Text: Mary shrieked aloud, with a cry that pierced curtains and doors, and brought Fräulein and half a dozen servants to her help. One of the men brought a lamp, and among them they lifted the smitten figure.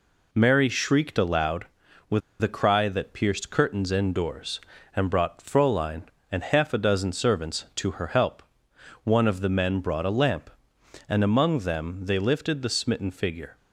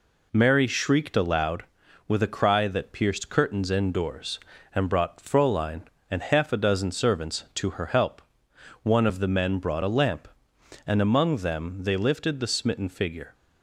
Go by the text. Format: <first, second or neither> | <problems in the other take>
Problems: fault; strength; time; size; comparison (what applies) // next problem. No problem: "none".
second | pauses between "with" and "a"; slight; at 2.2 s; 0.21 s long